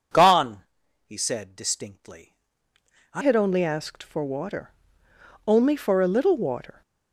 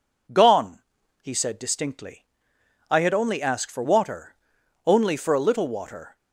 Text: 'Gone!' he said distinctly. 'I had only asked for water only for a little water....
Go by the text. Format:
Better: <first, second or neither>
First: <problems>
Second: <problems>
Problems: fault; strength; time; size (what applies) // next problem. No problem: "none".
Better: second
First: changes voice at "had"; from 3.2 s on; 3.6 s long // pauses between "water" and "only"; noticeable; at 4.6 s; 0.78 s long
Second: pauses between "water" and "only"; noticeable; at 4.3 s; 0.50 s long